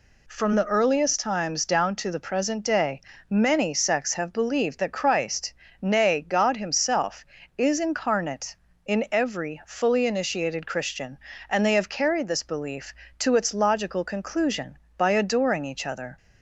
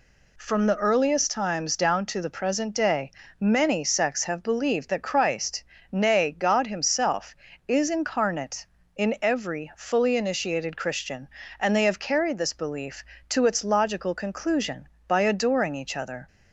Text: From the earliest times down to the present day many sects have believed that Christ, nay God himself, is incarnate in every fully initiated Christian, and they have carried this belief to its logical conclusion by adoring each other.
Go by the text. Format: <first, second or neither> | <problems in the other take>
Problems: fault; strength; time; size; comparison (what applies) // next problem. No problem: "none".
neither | pauses between "day" and "many"; slight; the same in both